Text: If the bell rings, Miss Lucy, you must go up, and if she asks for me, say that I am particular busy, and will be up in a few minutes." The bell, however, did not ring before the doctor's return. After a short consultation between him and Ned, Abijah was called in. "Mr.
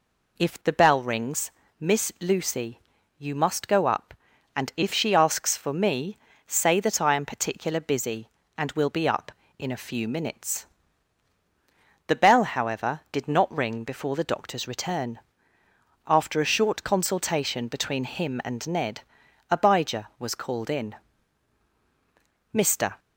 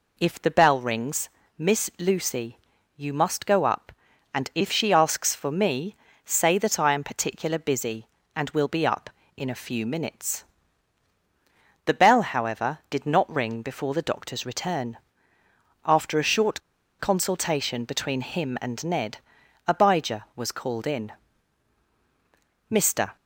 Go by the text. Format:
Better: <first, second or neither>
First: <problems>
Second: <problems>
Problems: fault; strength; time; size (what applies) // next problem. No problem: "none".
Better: first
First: none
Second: pauses between "short" and "consultation"; at 16.6 s; 0.39 s long